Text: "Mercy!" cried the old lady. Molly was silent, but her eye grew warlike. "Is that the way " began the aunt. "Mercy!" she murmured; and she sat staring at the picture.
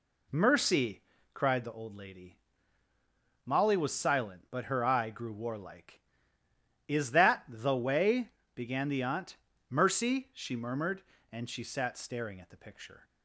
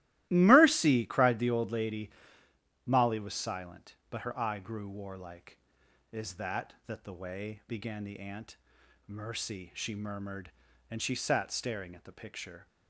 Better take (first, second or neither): first